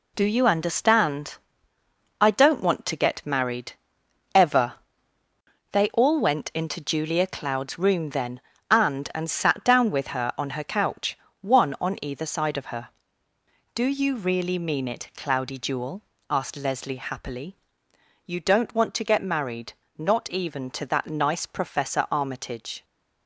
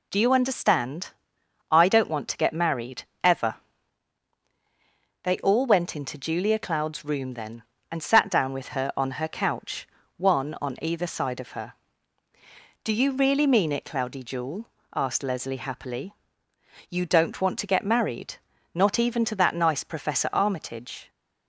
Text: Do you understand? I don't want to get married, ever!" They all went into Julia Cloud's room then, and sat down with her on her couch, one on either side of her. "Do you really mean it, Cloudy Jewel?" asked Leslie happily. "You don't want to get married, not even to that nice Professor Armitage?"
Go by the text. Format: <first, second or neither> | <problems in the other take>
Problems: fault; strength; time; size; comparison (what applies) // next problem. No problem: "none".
second | says "and" twice; at 9.1 s